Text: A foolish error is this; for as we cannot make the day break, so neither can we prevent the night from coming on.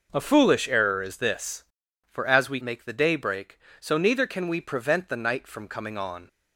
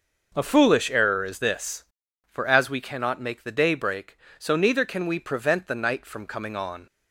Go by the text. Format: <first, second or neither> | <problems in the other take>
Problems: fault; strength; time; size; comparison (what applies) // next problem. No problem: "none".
second | skips "cannot"; at 2.6 s